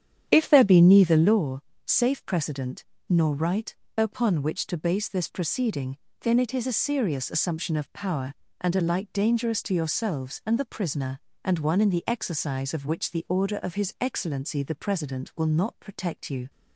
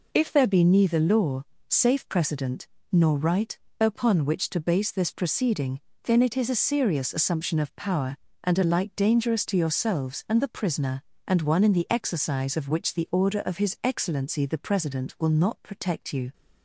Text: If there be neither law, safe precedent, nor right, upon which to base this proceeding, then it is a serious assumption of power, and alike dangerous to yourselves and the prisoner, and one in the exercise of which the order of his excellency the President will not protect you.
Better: second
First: starts louder than the rest; strong; until 1.5 s; 9.5 dB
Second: none

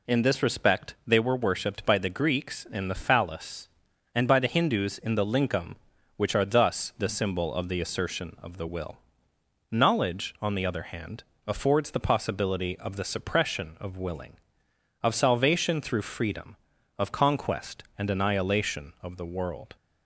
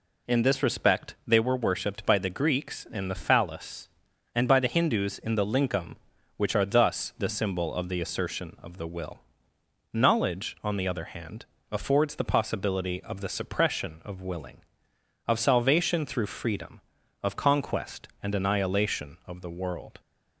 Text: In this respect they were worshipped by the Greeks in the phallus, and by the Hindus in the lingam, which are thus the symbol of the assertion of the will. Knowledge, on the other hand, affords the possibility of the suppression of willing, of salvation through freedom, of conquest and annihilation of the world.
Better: neither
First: none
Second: none

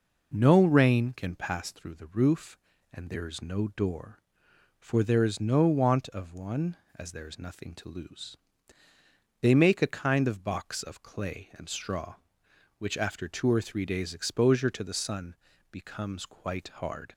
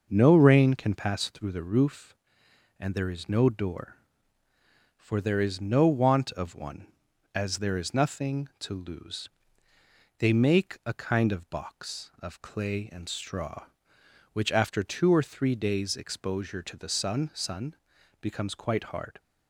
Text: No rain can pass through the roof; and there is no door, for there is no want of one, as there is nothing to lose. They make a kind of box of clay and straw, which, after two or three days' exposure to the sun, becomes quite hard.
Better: first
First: none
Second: says "sun" twice; at 17.3 s

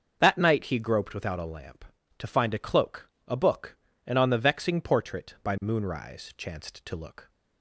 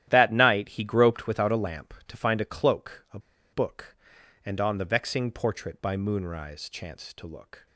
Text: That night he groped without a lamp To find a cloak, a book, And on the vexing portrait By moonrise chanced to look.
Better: first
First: starts louder than the rest; until 1.2 s; 6.5 dB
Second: starts louder than the rest; strong; until 1.0 s; 12.5 dB // pauses between "a" and "book"; slight; at 3.1 s; 0.34 s long

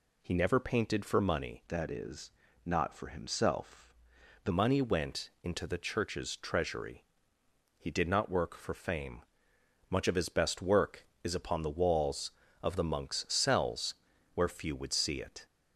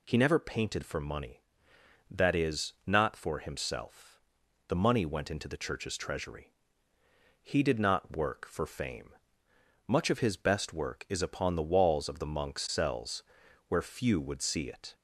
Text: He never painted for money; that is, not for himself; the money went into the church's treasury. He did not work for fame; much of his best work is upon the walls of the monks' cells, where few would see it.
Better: second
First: changes voice from "that" to "the"; from 1.6 to 4.5 s; 2.9 s long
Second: none

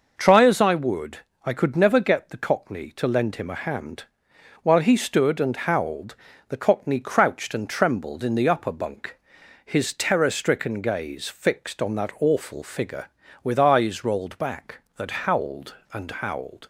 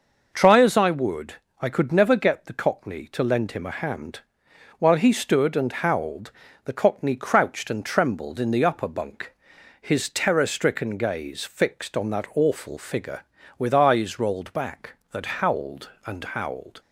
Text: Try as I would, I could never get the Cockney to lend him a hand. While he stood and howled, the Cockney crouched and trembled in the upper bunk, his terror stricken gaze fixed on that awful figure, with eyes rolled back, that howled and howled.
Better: neither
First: none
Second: none

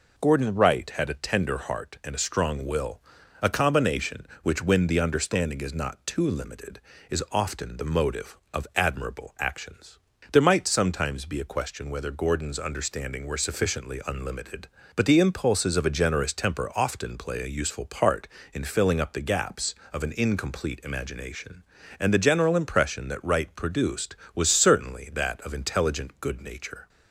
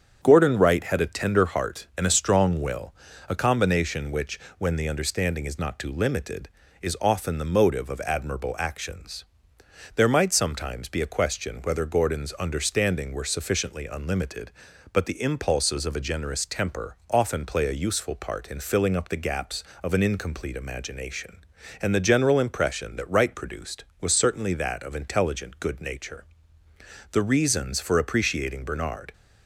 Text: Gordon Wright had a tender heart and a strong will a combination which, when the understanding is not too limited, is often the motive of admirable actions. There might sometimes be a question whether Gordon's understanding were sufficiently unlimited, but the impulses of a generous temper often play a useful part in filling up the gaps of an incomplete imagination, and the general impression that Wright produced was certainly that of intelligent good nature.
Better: first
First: pauses between "will" and "a"; at 3.0 s; 0.42 s long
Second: starts louder than the rest; strong; until 1.2 s; 8 dB // pauses between "will" and "a"; slight; at 2.9 s; 0.36 s long // goes on to say "The reasons for appreciating Bernard"; strong; from 27.1 s on; 2.0 s long

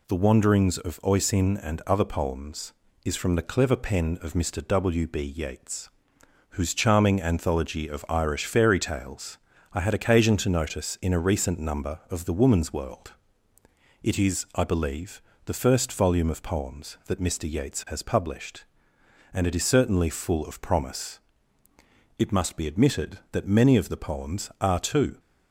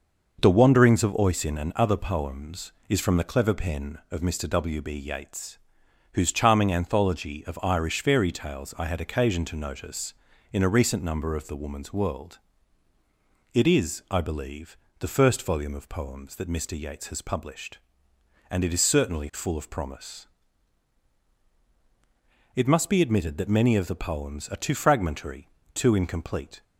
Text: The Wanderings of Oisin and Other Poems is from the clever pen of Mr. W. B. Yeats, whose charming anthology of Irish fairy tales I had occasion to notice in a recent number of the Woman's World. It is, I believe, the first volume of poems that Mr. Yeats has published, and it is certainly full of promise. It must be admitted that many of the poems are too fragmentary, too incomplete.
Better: second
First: pauses between "tales" and "I"; slight; at 9.3 s; 0.34 s long // stops before "fragmentary too incomplete"; at 25.1 s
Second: none

